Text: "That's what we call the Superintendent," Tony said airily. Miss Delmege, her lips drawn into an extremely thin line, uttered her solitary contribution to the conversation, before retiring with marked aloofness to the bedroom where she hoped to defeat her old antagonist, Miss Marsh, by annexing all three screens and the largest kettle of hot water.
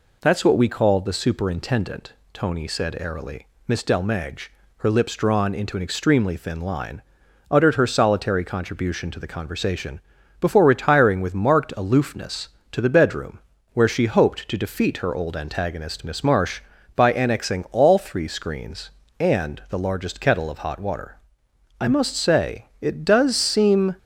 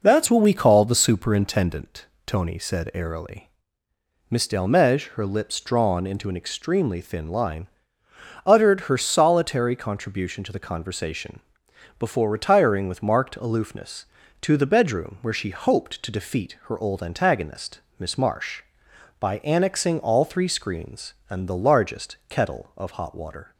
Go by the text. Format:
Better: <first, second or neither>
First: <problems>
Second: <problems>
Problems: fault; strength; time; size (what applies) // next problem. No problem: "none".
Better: second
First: pauses between "bedroom" and "where"; slight; at 13.3 s; 0.34 s long // goes on to say "I must say it does seem"; strong; from 21.7 s on; 2.1 s long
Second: none